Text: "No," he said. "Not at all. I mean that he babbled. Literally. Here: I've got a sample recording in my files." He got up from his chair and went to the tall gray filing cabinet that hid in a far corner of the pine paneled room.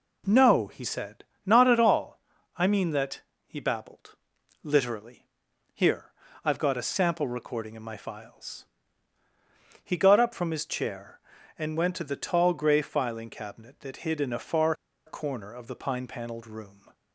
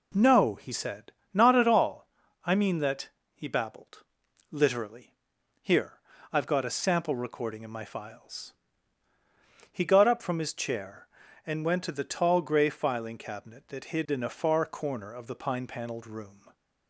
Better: second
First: pauses between "that" and "he"; slight; at 3.2 s; 0.24 s long // pauses between "far" and "corner"; slight; at 14.7 s; 0.33 s long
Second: pauses between "that" and "he"; slight; at 3.0 s; 0.24 s long

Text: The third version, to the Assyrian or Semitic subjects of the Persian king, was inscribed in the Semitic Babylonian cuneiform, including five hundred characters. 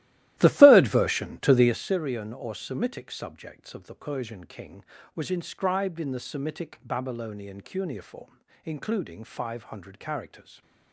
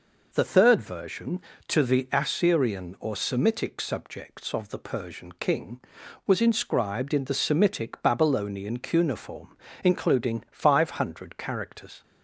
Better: second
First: starts louder than the rest; strong; until 1.8 s; 15 dB // stays silent after the last word; slight; from 10.4 s on; 0.5 s long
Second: none

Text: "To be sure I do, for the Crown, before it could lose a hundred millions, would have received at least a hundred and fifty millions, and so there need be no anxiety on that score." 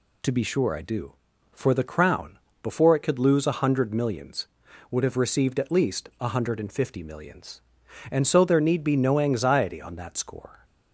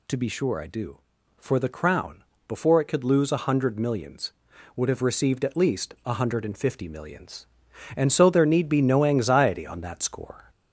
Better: first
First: none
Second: gets louder; slight; throughout; 2.5 dB

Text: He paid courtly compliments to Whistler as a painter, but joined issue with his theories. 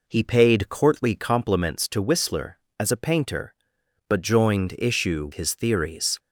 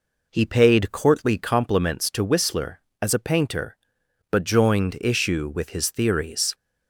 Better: second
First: skips "with"; at 5.3 s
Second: none

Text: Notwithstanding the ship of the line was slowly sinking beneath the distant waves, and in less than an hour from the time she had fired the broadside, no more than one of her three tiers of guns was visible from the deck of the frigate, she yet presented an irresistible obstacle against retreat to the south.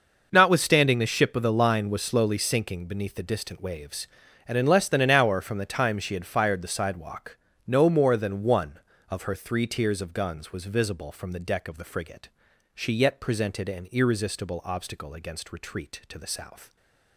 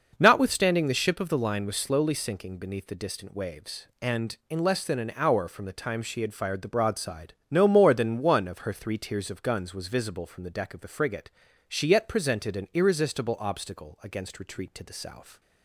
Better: second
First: says "sidewalk" for "broadside"; at 6.6 s // stays silent after the last word; slight; from 16.6 s on; 0.5 s long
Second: none

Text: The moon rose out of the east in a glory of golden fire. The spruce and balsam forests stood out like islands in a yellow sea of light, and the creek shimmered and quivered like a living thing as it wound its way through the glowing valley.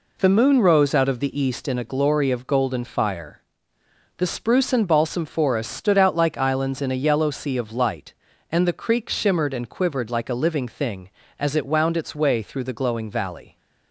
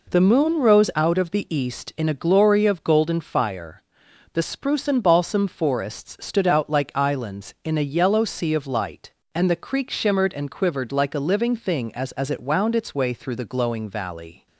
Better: first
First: none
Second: says "as" twice; at 12.1 s

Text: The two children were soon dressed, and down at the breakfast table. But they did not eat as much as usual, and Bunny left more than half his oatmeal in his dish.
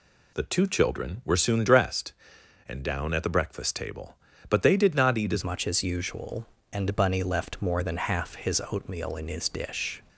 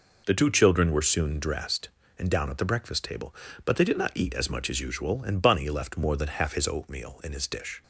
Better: second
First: changes voice at "much"; from 5.4 s on; 4.6 s long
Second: none

